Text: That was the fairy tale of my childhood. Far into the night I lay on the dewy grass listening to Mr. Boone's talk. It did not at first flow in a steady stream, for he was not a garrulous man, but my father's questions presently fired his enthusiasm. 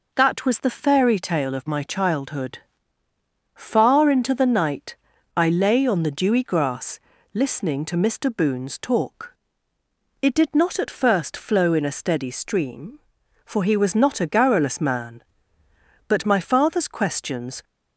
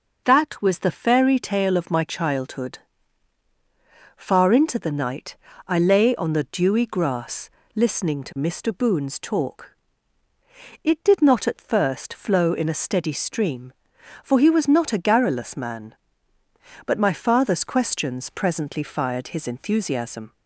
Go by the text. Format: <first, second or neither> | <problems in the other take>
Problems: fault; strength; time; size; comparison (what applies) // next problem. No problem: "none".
second | pauses between "night" and "I"; at 4.9 s; 0.40 s long; slight in the second // pauses between "grass" and "listening"; slight; at 7.0 s; 0.32 s long; slight in the second // stops before "presently fired his enthusiasm"; at 17.6 s